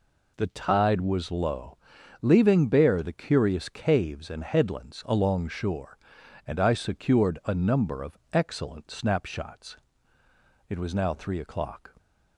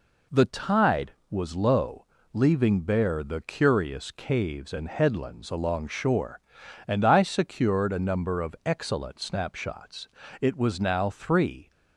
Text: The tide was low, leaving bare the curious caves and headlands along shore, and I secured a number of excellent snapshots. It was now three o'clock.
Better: first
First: none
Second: stops before "o'clock"; at 11.7 s

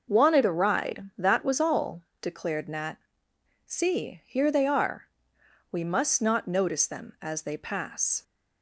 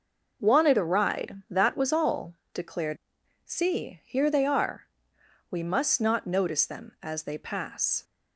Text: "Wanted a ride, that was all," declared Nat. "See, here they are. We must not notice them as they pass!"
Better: first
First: none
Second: skips "Nat"; at 3.2 s

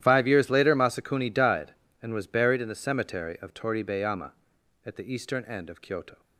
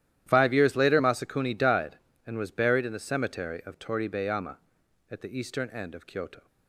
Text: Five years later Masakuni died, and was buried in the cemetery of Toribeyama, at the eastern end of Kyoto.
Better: neither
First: starts louder than the rest; strong; until 1.0 s; 12 dB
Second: starts louder than the rest; strong; until 1.2 s; 12 dB

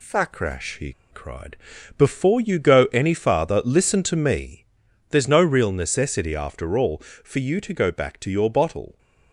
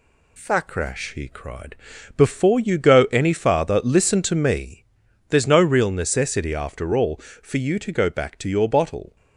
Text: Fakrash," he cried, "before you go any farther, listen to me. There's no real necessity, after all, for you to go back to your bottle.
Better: second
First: pauses between "he" and "cried"; slight; at 0.9 s; 0.18 s long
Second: none

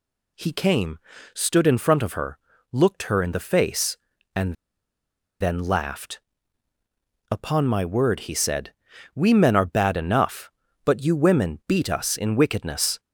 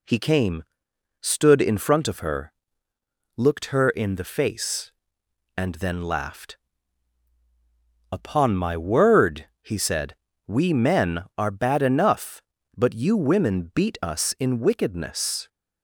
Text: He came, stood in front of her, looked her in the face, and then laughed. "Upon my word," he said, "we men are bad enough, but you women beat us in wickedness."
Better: second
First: pauses between "and" and "then"; noticeable; at 4.5 s; 0.86 s long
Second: none

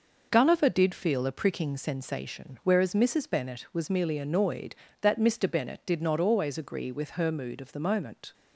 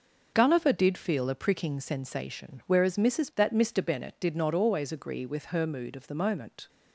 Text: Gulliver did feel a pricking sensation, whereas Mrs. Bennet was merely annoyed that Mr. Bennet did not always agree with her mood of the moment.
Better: first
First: none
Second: starts louder than the rest; until 1.3 s; 6.5 dB // skips "Bennet was merely annoyed"; at 3.3 s

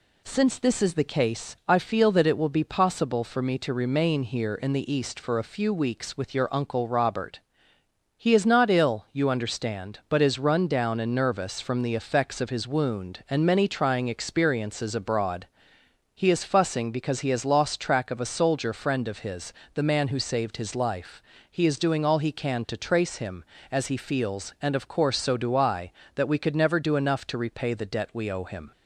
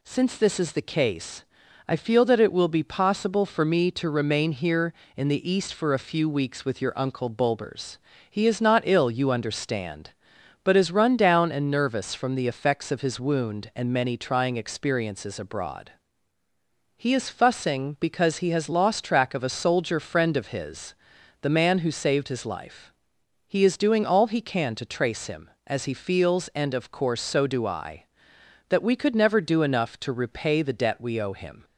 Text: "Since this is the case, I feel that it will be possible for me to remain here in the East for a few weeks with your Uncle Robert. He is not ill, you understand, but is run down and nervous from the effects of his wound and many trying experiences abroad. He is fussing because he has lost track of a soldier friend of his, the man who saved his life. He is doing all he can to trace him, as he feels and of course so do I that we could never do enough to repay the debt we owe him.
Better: first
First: none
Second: says "Bulbers" for "Robert"; at 7.2 s

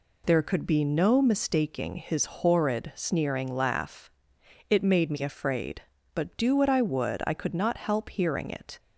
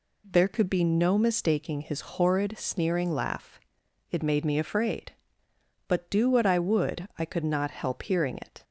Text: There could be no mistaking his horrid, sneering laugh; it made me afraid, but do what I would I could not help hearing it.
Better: neither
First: none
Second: none

